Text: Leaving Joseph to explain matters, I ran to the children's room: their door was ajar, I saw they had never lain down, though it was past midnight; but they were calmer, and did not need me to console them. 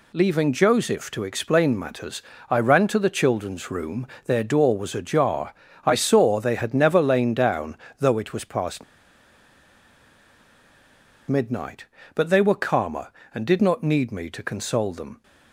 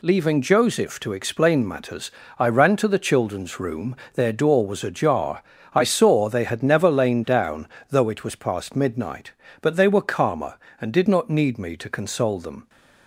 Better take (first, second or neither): second